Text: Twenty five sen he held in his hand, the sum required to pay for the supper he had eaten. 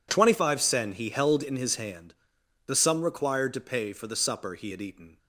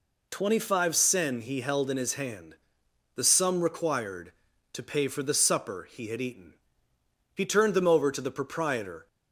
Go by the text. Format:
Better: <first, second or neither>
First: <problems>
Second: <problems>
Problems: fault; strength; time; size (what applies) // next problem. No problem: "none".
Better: first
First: none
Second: goes on to say "He turned them over to the proprietor"; strong; from 7.3 s on; 1.7 s long